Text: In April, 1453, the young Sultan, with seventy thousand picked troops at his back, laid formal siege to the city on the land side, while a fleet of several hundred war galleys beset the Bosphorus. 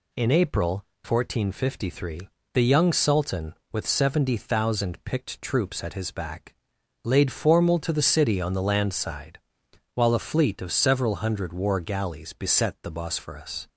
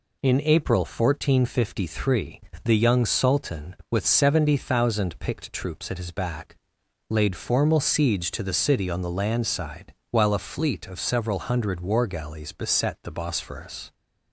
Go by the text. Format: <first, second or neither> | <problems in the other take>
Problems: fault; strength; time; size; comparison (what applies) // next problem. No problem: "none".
second | skips "siege"; at 7.7 s